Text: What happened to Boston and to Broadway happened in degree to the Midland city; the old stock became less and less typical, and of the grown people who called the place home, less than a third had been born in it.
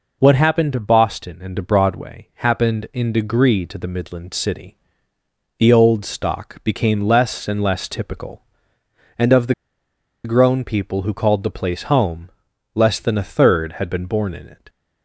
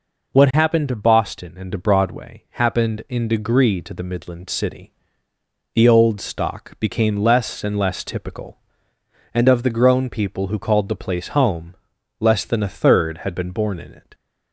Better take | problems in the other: second | pauses between "the" and "grown"; noticeable; at 9.5 s; 0.71 s long

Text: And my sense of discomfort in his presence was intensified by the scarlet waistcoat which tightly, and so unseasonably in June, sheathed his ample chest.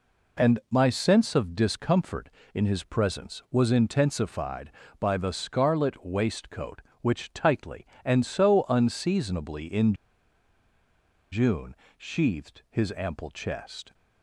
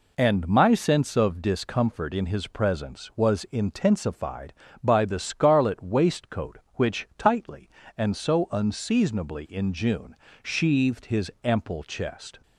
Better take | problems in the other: second | pauses between "in" and "June"; strong; at 9.9 s; 1.3 s long

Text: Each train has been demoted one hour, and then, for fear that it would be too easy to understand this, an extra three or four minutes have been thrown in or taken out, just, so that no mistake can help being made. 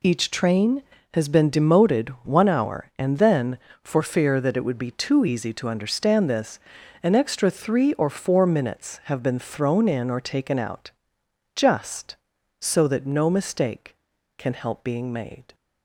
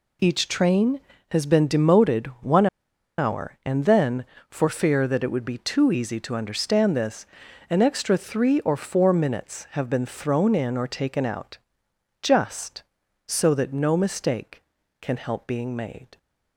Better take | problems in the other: first | pauses between "demoted" and "one"; slight; at 2.2 s; 0.16 s long; slight in the first // pauses between "one" and "hour"; noticeable; at 2.6 s; 0.51 s long

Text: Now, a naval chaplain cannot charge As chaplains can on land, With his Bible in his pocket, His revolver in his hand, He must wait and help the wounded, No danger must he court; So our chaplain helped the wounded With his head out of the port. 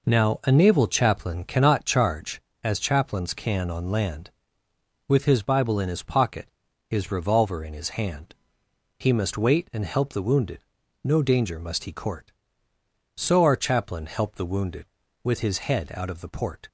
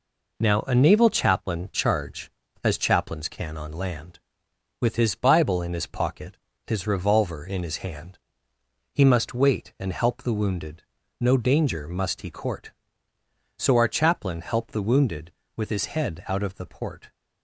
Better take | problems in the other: first | skips "cannot"; at 1.7 s

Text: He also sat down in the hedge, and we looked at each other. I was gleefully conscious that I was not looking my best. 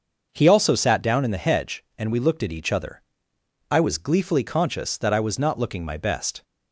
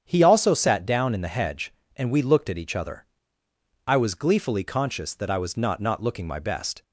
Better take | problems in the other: first | starts louder than the rest; strong; until 1.0 s; 8.5 dB; also in the first // says "not" twice; at 5.8 s

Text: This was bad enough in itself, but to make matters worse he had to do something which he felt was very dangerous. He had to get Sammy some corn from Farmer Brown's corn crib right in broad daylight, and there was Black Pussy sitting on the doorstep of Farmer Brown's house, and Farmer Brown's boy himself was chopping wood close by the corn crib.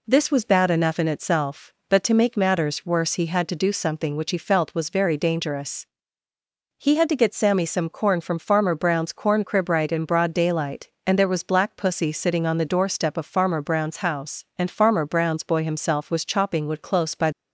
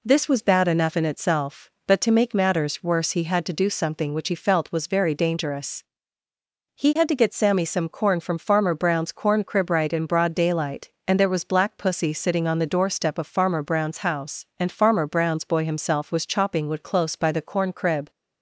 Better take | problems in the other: second | stops before "the corn crib"; at 17.3 s

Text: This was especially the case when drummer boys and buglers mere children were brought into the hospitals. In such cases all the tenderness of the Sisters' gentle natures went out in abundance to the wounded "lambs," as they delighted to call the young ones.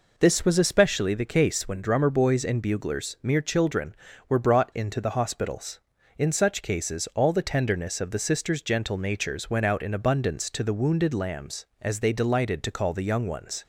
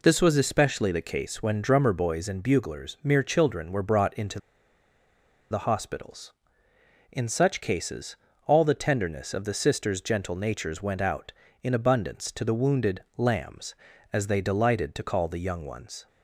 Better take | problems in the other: first | pauses between "into" and "the"; at 4.3 s; 1.1 s long // pauses between "cases" and "all"; slight; at 8.1 s; 0.30 s long // pauses between "wounded" and "lambs"; slight; at 13.0 s; 0.16 s long

